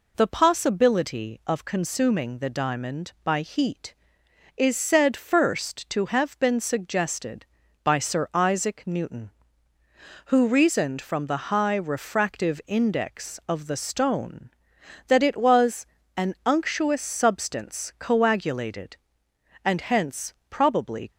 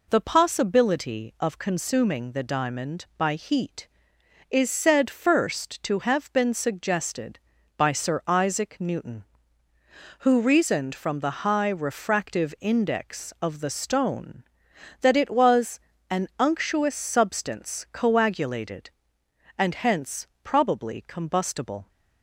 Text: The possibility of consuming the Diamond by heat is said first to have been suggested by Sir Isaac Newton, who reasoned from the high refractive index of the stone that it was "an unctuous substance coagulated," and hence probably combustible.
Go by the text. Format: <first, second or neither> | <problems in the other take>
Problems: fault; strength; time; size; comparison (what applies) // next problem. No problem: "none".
second | pauses between "was" and "an"; slight; at 15.8 s; 0.30 s long; slight in the second // pauses between "hence" and "probably"; slight; at 20.3 s; 0.16 s long; slight in the second // stops before "combustible"; at 21.1 s